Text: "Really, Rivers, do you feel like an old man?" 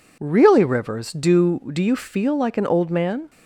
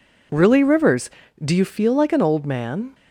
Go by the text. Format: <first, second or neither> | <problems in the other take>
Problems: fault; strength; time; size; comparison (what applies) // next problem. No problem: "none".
second | says "do" twice; at 1.7 s